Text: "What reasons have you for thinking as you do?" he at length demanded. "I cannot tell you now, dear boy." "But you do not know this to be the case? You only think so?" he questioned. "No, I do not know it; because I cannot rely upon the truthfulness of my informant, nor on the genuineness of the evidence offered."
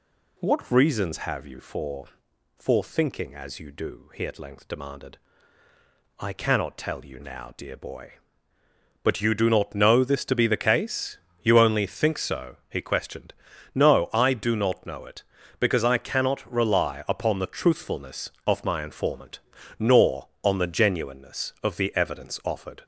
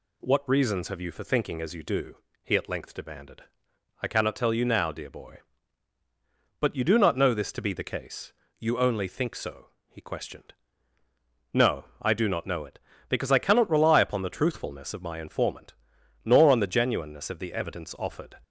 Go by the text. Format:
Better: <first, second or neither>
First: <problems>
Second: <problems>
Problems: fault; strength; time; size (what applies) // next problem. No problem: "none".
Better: second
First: says "for" twice; at 2.5 s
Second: none